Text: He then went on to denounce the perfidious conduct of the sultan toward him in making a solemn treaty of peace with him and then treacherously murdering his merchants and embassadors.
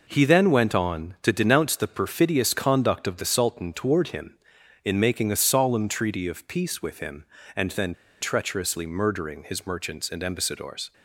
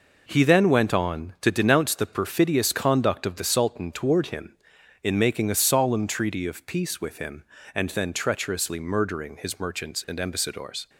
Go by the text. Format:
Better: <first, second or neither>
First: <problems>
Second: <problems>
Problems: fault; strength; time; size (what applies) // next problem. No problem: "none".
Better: second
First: pauses between "then" and "treacherously"; slight; at 7.9 s; 0.27 s long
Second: none